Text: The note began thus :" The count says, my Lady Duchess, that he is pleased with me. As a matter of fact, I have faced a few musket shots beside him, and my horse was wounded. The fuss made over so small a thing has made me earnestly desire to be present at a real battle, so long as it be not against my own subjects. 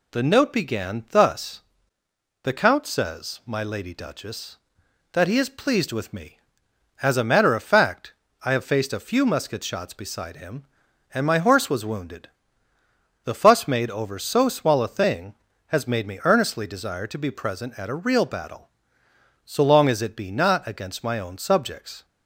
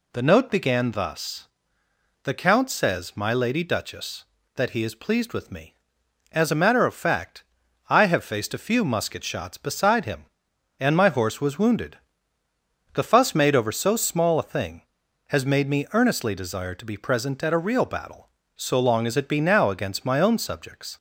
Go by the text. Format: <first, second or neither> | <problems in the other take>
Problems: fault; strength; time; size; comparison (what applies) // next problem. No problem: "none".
first | says "now" for "not"; at 19.4 s